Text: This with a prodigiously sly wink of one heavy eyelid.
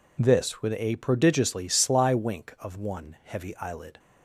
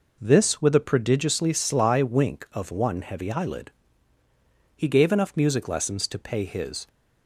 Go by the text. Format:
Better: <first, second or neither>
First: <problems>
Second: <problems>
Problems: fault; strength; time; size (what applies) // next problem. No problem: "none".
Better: first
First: none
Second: goes on to say "He gave enough music lessons to pay his"; strong; from 4.7 s on; 2.1 s long